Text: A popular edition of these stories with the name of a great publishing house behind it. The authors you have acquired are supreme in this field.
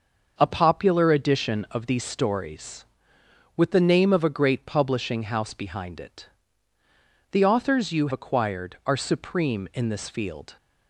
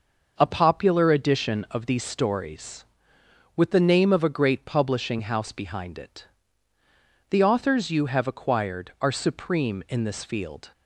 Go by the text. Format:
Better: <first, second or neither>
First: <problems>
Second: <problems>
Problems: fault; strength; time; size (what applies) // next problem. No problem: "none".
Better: second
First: starts louder than the rest; until 1.3 s; 6.5 dB // skips "have"; at 8.1 s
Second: starts louder than the rest; noticeable; until 1.3 s; 6 dB